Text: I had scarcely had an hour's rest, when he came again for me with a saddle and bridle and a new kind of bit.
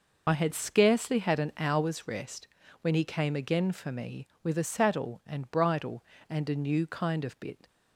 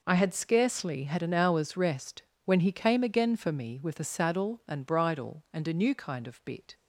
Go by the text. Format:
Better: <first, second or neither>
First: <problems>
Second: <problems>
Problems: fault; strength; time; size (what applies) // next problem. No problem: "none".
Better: second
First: loses the start of "I"; at 0.2 s; 40 ms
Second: none